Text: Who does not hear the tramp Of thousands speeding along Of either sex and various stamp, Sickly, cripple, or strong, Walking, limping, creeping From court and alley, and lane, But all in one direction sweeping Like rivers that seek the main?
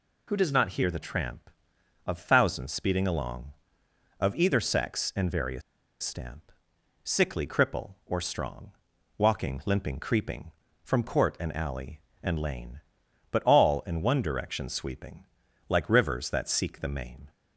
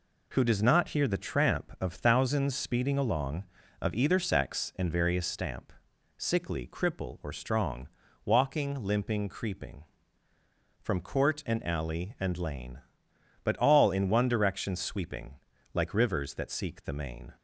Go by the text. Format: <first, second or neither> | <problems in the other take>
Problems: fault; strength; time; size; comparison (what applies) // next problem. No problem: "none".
second | pauses between "various" and "stamp"; at 5.6 s; 0.41 s long // pauses between "sweeping" and "Like"; noticeable; at 15.2 s; 0.46 s long; also in the second